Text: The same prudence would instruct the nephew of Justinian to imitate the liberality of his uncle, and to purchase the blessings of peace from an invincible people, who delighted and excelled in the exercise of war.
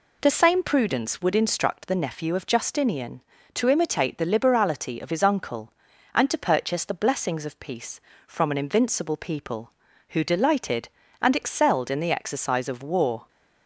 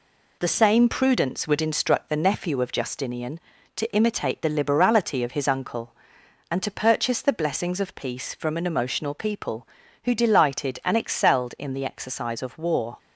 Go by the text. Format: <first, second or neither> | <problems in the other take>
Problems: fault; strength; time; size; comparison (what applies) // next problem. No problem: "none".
first | says "emotional" for "invincible"; at 8.6 s